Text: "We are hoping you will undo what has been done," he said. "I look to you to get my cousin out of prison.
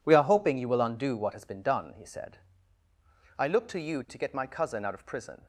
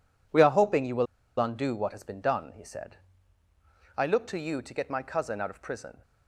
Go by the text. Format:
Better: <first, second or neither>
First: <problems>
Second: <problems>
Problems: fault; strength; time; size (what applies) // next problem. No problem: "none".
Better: first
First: none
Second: pauses between "will" and "undo"; slight; at 1.0 s; 0.33 s long